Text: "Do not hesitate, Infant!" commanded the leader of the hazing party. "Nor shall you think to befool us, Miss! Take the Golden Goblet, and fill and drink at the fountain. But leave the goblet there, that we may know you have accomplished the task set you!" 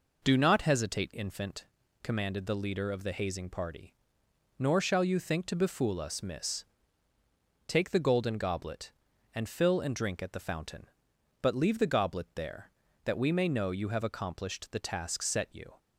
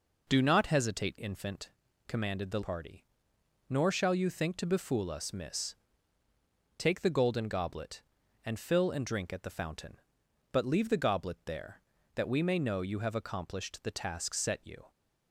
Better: first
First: none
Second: skips "leader of the hazing"; at 2.6 s

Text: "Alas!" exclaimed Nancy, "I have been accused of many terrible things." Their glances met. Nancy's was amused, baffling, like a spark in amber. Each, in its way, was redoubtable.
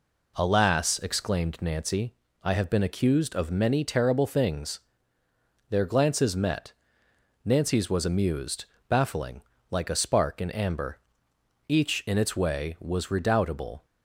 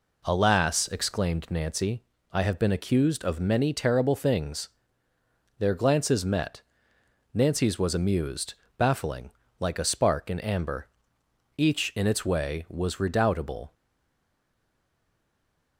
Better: first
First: none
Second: stays silent after the last word; noticeable; from 13.7 s on; 2.0 s long

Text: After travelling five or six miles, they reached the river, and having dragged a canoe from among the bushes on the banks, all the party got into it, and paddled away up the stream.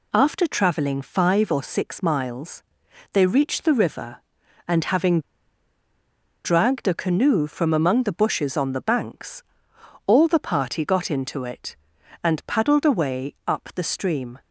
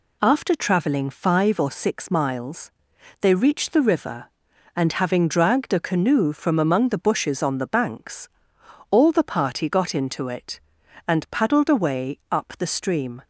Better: second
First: pauses between "having" and "dragged"; at 5.2 s; 1.2 s long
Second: none

